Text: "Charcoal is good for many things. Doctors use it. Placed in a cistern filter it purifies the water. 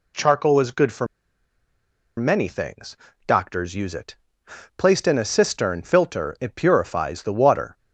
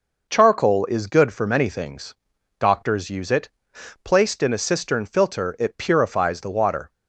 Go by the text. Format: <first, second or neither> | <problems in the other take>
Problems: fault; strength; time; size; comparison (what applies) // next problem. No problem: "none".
second | pauses between "for" and "many"; at 1.0 s; 1.1 s long